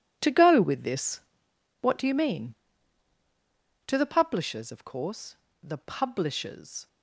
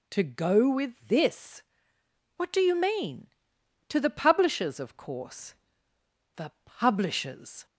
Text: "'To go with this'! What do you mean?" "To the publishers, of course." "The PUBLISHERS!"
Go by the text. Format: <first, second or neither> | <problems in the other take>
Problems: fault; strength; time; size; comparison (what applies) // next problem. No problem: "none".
second | gets quieter; strong; throughout; 13.5 dB